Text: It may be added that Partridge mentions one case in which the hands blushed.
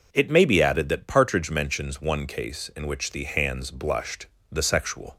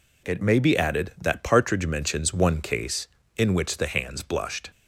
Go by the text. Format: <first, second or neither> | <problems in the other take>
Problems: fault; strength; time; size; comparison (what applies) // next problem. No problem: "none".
second | goes on to say "The sexual"; noticeable; from 4.5 s on; 0.66 s long